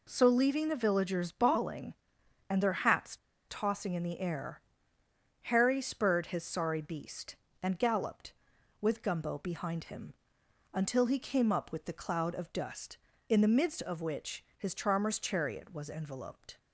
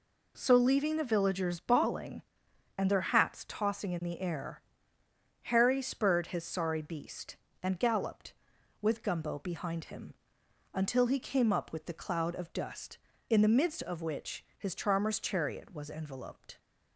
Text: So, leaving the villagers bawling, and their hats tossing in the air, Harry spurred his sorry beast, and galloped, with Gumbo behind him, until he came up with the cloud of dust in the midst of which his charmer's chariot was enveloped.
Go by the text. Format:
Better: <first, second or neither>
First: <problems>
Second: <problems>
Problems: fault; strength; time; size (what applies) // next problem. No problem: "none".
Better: second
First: pauses between "hats" and "tossing"; slight; at 3.1 s; 0.31 s long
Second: none